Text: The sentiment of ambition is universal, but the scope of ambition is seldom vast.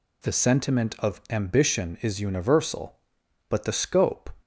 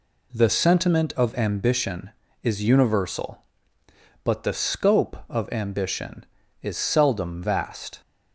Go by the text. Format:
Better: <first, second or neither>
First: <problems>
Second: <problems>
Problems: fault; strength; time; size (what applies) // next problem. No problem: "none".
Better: second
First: stops before "of ambition is seldom vast"; at 4.4 s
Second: none